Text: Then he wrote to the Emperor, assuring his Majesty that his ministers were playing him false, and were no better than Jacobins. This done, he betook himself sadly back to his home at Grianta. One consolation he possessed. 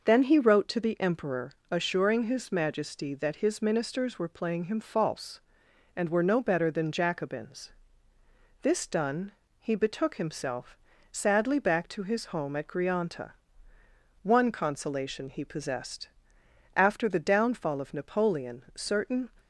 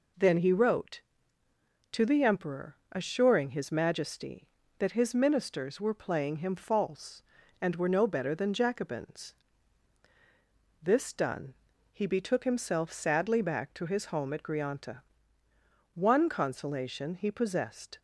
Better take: second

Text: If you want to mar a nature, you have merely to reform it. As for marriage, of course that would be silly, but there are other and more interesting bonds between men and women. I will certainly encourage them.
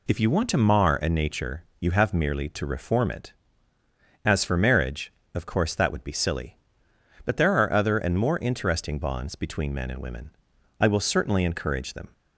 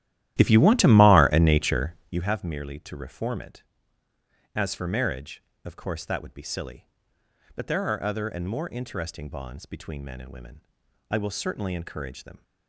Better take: first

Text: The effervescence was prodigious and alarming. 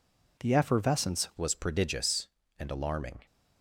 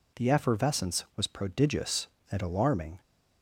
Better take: second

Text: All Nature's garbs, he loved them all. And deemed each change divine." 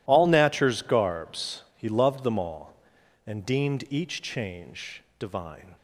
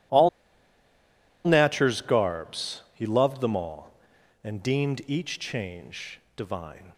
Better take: first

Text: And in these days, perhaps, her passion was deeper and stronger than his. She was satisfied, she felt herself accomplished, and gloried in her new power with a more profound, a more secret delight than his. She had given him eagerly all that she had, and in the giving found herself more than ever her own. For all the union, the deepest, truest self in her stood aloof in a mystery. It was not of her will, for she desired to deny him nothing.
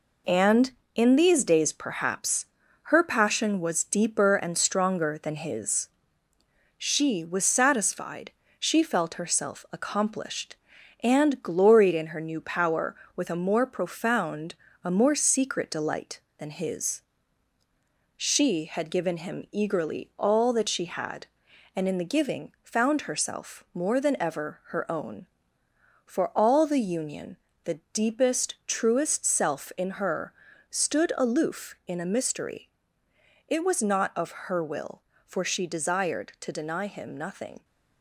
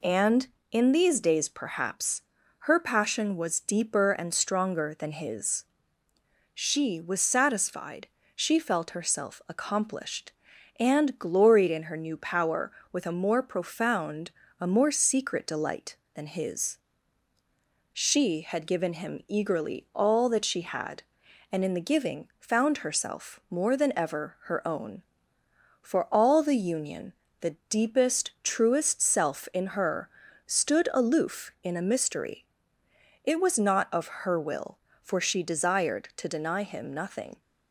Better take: second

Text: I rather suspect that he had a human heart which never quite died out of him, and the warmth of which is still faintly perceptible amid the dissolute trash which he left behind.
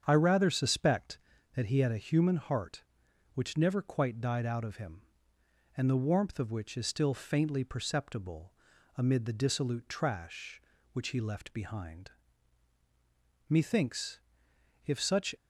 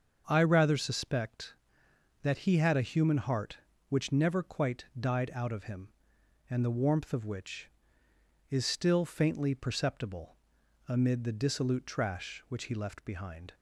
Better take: second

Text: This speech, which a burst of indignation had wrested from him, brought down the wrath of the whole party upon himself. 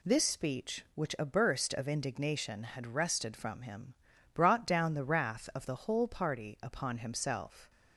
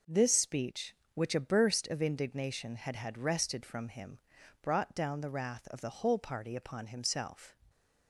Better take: first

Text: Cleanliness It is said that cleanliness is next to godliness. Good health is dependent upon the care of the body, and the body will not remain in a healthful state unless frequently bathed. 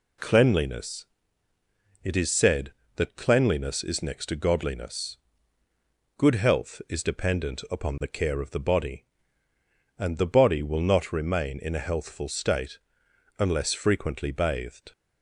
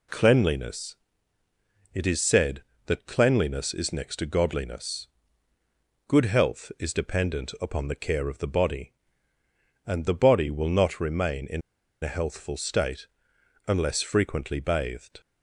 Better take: first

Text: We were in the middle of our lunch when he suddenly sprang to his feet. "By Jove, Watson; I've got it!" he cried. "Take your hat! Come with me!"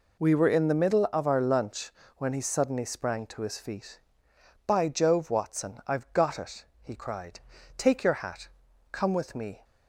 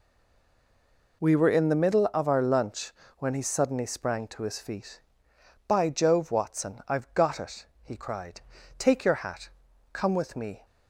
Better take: first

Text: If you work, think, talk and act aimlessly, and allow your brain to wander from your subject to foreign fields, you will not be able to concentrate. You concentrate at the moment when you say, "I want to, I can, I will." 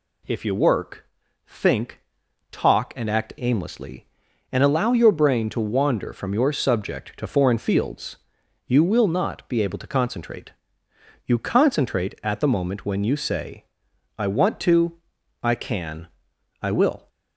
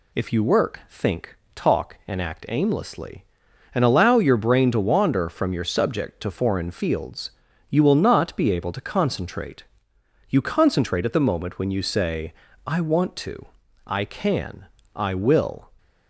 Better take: neither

